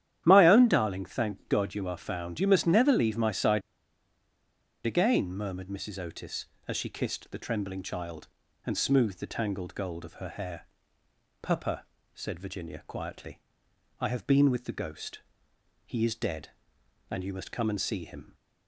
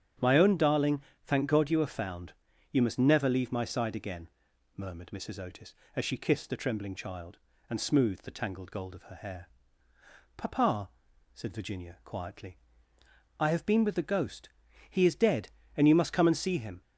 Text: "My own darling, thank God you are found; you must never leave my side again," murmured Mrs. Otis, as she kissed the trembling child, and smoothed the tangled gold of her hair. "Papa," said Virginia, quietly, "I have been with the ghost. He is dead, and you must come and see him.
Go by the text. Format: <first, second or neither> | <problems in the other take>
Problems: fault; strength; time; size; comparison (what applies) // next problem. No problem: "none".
second | starts louder than the rest; strong; until 1.2 s; 10.5 dB; strong in the second // pauses between "side" and "again"; at 3.6 s; 1.2 s long